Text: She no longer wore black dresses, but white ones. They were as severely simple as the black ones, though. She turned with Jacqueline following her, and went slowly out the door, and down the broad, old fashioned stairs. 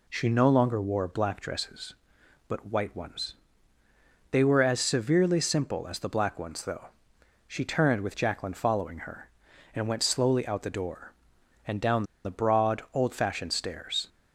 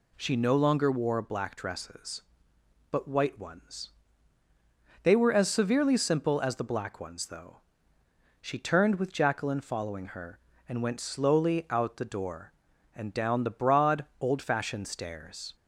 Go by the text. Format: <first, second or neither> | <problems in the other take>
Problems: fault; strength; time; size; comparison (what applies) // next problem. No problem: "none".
second | pauses between "down" and "the"; slight; at 12.0 s; 0.21 s long